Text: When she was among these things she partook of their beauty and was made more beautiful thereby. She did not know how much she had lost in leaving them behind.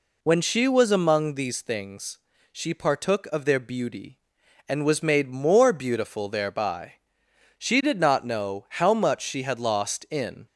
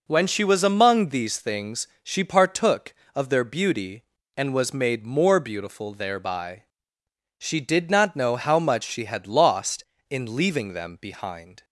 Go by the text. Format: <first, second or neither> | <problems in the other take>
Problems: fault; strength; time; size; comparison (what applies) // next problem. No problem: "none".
second | pauses between "things" and "she"; slight; at 2.1 s; 0.34 s long; slight in the second // stops before "leaving them behind"; at 10.4 s